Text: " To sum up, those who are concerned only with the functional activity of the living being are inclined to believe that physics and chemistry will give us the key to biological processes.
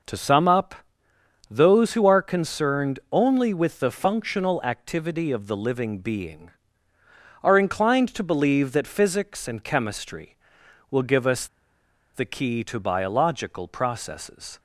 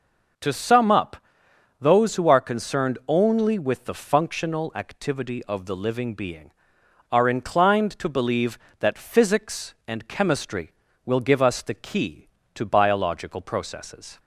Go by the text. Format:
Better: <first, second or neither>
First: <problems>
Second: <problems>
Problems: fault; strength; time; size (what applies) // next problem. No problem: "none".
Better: second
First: pauses between "us" and "the"; noticeable; at 11.4 s; 0.68 s long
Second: none